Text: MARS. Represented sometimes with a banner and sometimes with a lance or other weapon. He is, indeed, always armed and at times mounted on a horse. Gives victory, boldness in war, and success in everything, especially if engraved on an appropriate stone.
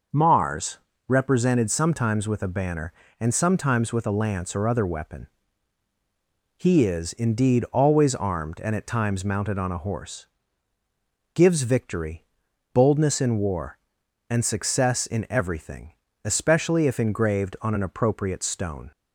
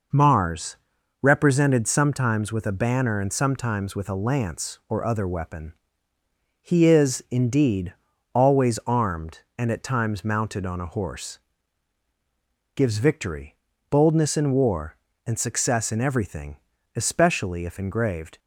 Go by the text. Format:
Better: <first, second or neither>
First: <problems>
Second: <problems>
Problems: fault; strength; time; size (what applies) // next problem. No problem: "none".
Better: first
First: none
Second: stops before "on an appropriate stone"; at 18.3 s